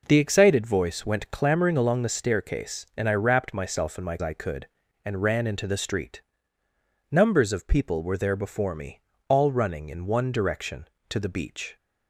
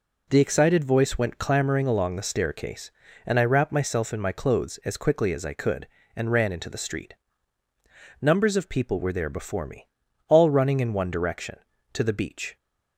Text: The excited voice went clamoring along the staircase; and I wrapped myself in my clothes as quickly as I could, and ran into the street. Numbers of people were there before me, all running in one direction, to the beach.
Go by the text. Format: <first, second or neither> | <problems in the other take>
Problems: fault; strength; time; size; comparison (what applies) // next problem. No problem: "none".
second | skips "clothes as quickly as"; at 4.1 s